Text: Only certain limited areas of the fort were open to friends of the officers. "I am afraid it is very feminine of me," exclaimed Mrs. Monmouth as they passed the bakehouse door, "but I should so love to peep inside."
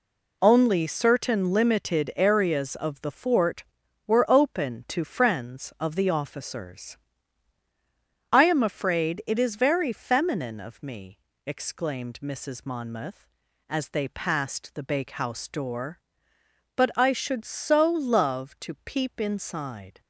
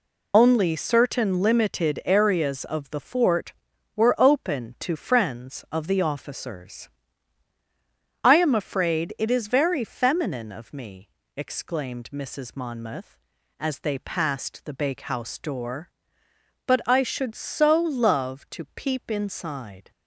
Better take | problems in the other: first | loses the start of "Only"; at 0.3 s; 45 ms

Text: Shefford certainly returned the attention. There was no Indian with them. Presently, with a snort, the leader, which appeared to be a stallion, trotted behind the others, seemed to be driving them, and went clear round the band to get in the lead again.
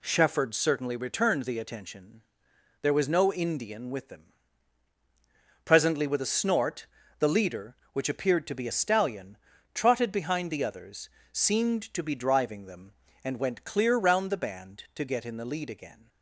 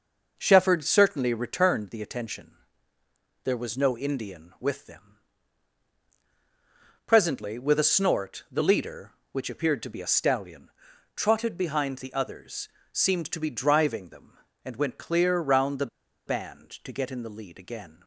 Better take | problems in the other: first | pauses between "the" and "band"; at 15.8 s; 0.40 s long

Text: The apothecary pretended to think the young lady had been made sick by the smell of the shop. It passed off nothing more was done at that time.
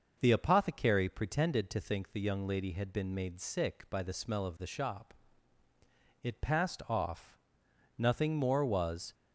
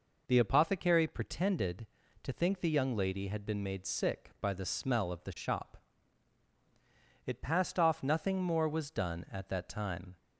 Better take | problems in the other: second | pauses between "off" and "nothing"; noticeable; at 7.3 s; 0.60 s long // stops before "done at that time"; at 9.1 s

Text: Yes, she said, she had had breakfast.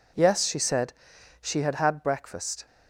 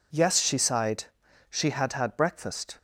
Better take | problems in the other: first | says "sighed" for "said"; at 0.5 s

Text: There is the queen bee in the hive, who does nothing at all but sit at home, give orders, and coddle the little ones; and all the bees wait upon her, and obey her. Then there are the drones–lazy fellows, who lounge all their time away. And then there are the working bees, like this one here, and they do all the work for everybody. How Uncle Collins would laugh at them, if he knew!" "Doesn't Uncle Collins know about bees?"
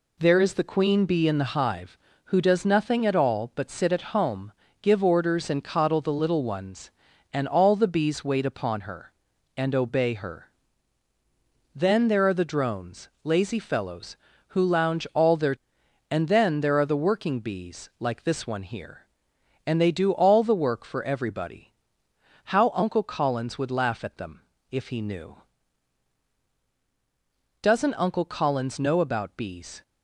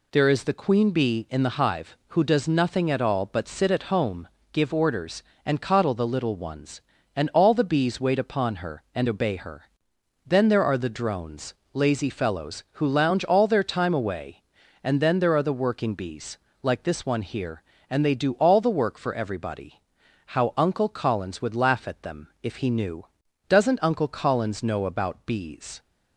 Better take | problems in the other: second | skips "time away"; at 15.8 s

